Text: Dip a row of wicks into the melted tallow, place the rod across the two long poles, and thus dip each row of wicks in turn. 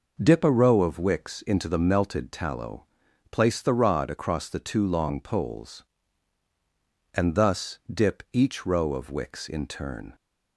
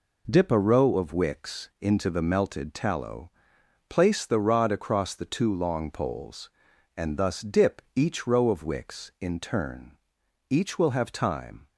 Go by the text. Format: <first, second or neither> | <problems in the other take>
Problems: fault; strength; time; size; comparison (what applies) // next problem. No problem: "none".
first | goes on to say "Each will have time"; noticeable; from 10.5 s on; 1.1 s long